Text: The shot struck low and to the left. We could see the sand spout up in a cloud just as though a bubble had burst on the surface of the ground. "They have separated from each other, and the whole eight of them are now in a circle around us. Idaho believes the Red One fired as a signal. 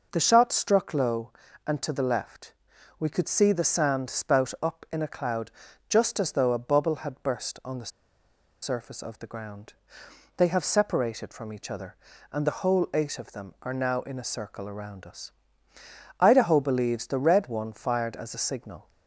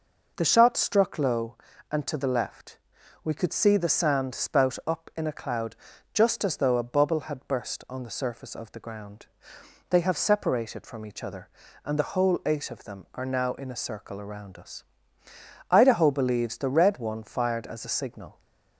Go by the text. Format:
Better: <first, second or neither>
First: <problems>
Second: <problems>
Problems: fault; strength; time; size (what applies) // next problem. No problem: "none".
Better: second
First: pauses between "cloud" and "just"; slight; at 5.5 s; 0.36 s long // pauses between "the" and "surface"; noticeable; at 7.9 s; 0.72 s long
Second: pauses between "cloud" and "just"; slight; at 5.7 s; 0.36 s long